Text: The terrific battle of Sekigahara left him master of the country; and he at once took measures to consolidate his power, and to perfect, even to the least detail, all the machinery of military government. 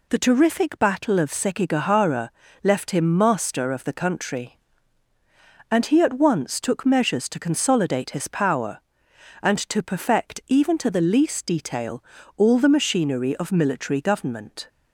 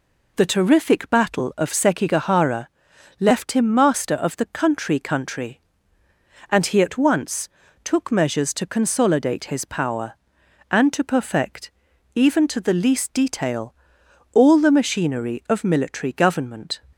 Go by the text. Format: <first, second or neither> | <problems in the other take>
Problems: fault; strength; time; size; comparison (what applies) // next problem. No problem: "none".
first | pauses between "Sekigahara" and "left"; noticeable; at 2.6 s; 0.52 s long; slight in the first // says "country" twice; at 4.9 s // pauses between "once" and "took"; slight; at 7.4 s; 0.34 s long